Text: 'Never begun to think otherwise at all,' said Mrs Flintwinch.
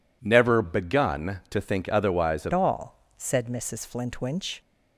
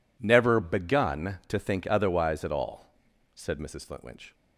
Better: second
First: changes voice at "all"; from 2.5 s on; 2.1 s long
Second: none

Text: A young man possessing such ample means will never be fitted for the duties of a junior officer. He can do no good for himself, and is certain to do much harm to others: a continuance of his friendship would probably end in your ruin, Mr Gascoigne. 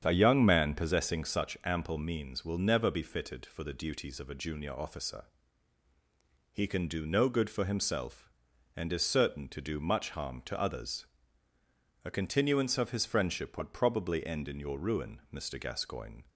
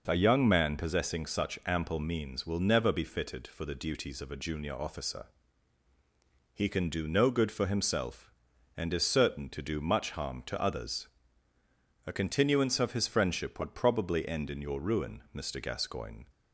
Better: second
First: starts louder than the rest; strong; until 1.5 s; 8 dB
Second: none

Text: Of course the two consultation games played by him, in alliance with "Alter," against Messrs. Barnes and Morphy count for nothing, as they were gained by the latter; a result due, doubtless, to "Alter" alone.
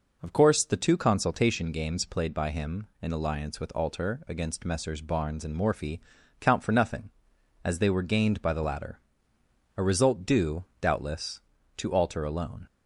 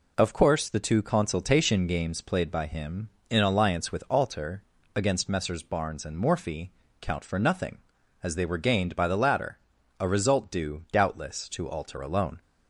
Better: neither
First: pauses between "Morphy" and "count"; at 6.0 s; 0.40 s long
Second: pauses between "Morphy" and "count"; slight; at 6.7 s; 0.30 s long

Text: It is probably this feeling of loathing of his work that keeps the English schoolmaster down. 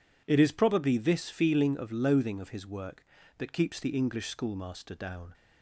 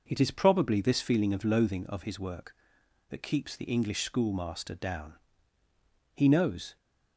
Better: first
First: none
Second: goes on to say "He knows"; noticeable; from 6.1 s on; 0.62 s long

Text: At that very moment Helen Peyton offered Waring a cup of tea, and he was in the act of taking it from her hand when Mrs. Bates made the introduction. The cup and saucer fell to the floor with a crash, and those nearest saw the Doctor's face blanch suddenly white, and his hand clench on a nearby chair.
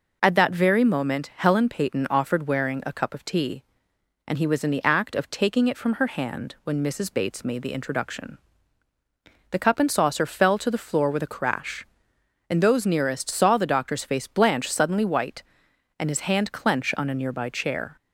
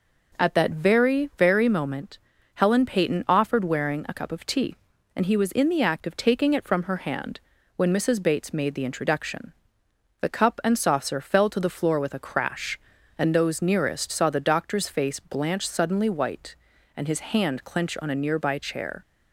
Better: first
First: none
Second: says "very" twice; at 1.3 s // pauses between "moment" and "Helen"; at 2.1 s; 0.38 s long // pauses between "hand" and "when"; at 7.3 s; 0.38 s long

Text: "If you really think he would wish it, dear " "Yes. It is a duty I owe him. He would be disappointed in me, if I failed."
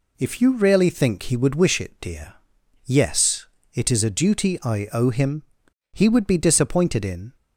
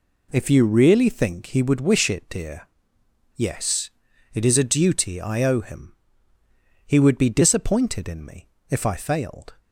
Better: second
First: stops before "me if I failed"; at 7.3 s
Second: none

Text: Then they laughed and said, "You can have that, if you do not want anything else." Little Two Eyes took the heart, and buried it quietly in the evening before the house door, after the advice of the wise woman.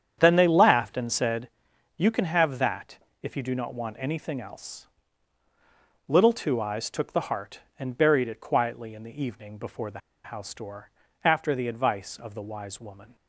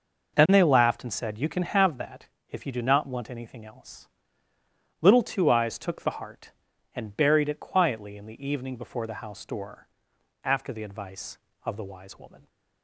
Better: second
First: starts louder than the rest; strong; until 1.1 s; 8.5 dB // pauses between "the" and "house"; slight; at 9.9 s; 0.25 s long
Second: none

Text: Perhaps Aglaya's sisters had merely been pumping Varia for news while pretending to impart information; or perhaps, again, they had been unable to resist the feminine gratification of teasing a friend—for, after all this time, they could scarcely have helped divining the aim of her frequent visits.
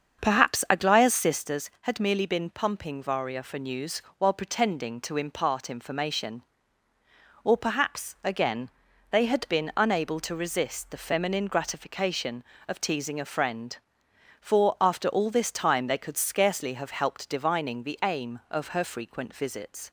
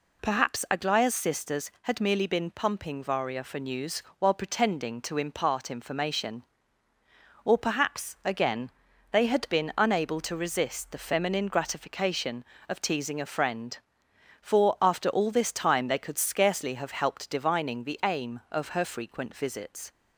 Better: second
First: starts louder than the rest; until 1.5 s; 7 dB // pauses between "news" and "while"; slight; at 4.0 s; 0.16 s long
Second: pauses between "news" and "while"; slight; at 4.0 s; 0.16 s long

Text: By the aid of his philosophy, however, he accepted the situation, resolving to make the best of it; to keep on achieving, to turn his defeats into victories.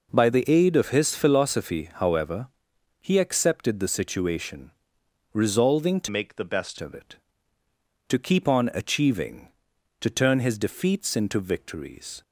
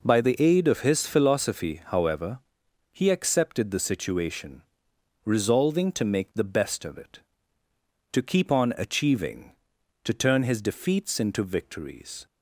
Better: second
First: changes voice from "make" to "best"; from 6.0 to 6.7 s; 0.7 s long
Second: none

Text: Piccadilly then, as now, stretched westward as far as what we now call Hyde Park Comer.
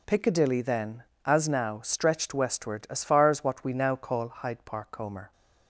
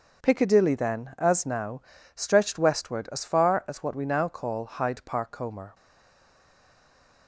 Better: first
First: none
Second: stays silent after the last word; noticeable; from 5.7 s on; 1.5 s long

